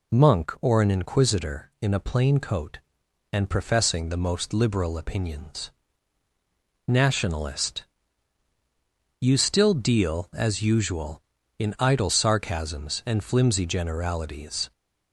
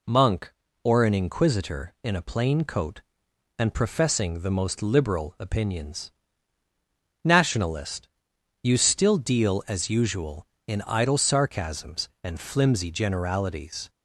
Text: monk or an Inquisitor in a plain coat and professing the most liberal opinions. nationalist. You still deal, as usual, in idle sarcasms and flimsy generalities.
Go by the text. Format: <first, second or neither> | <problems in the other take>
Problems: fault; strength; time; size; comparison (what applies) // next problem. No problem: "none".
neither | none